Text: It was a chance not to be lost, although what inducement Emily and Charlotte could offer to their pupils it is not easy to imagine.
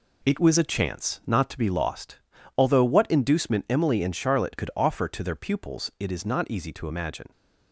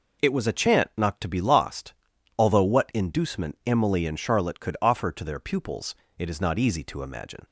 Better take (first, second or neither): first